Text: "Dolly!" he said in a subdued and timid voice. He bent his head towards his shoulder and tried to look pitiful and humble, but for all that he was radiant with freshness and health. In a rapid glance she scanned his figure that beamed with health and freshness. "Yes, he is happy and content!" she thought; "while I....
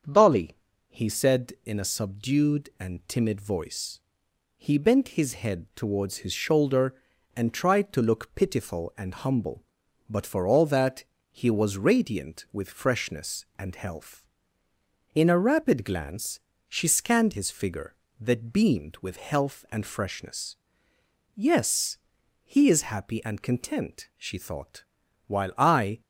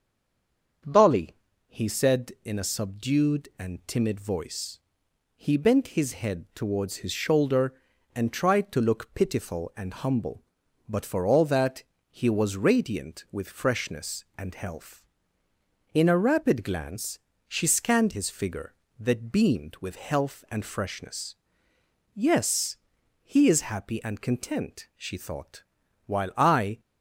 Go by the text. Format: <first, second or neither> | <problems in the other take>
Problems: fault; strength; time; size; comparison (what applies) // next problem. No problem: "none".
first | stays silent before the first word; slight; until 0.8 s; 0.8 s long // starts louder than the rest; until 2.2 s; 7 dB; also in the first // pauses between "that" and "he"; slight; at 11.8 s; 0.26 s long; slight in the first // pauses between "glance" and "she"; slight; at 17.1 s; 0.28 s long; slight in the first